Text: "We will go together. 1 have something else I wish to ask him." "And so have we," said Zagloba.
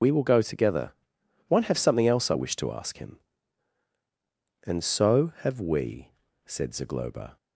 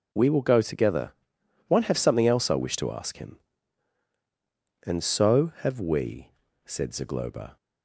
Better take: second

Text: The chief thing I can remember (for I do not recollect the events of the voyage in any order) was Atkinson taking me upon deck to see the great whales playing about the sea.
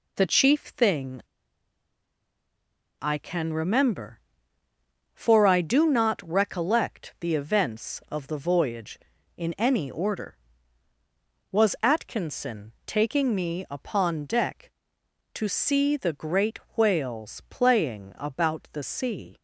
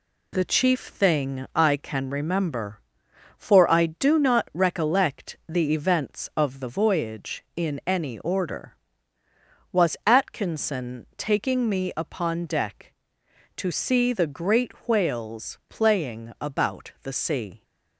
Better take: second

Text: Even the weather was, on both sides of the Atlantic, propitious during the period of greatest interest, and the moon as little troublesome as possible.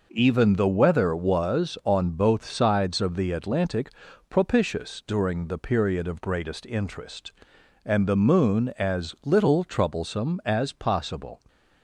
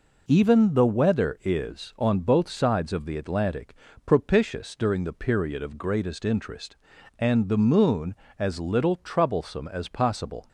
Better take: first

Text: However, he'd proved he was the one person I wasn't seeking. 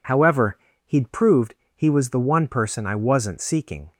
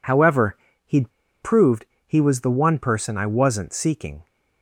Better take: first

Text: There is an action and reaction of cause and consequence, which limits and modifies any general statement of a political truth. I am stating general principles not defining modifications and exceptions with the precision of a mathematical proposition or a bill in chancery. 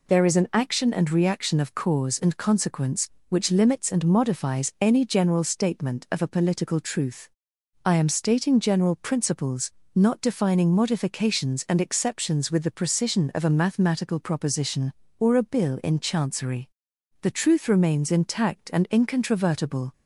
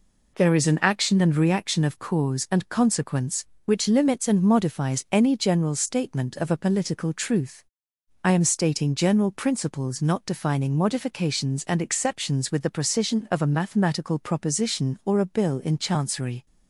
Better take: second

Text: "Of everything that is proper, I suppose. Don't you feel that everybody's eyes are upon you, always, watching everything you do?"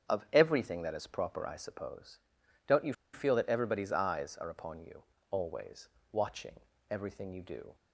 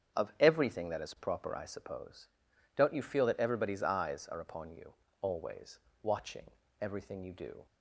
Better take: second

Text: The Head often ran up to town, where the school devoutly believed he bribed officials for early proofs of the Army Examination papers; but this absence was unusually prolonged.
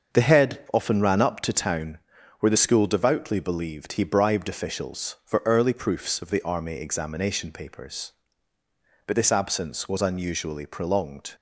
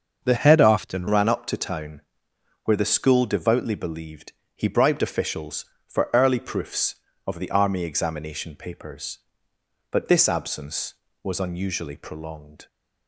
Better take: first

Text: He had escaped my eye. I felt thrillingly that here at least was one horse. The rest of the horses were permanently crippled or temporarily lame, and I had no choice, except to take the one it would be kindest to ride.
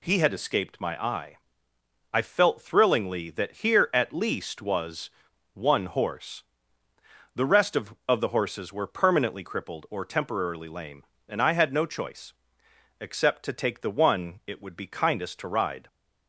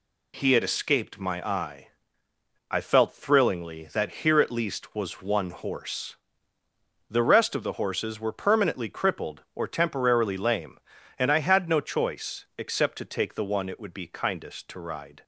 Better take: second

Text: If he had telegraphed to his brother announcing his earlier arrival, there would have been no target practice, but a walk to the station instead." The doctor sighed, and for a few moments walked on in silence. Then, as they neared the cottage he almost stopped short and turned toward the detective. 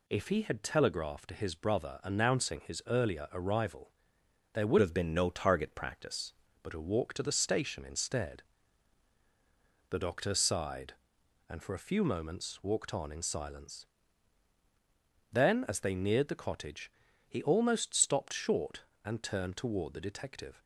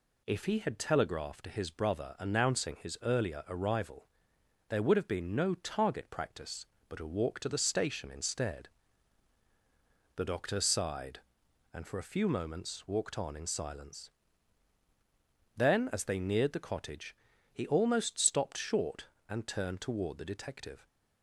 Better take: second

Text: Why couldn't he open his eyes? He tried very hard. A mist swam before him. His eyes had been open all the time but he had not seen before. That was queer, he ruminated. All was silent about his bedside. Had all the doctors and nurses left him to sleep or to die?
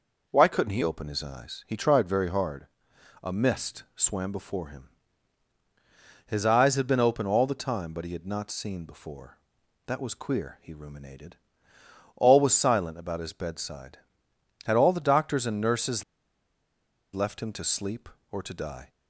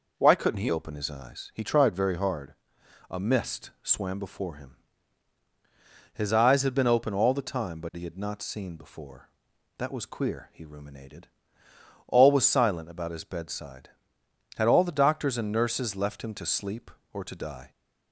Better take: second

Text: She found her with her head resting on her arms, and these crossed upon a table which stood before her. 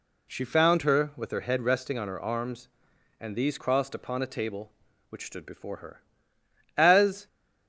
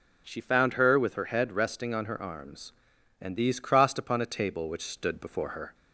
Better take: second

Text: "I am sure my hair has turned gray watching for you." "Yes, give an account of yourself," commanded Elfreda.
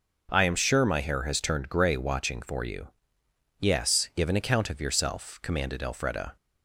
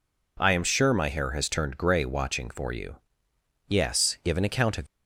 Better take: first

